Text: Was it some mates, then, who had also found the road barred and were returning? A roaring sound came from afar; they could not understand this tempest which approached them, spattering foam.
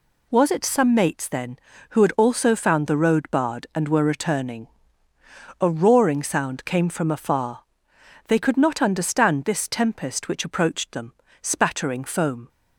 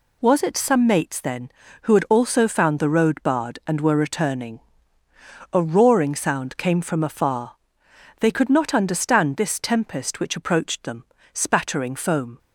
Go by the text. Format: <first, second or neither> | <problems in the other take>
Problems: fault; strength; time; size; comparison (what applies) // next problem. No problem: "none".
neither | none